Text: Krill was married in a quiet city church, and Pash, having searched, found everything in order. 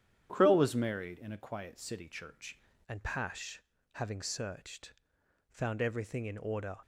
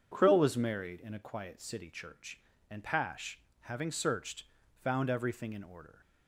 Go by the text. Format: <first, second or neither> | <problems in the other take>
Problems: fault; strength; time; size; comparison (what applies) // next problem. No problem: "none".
second | starts louder than the rest; strong; until 1.3 s; 9.5 dB // changes voice at "and"; from 2.8 s on; 3.9 s long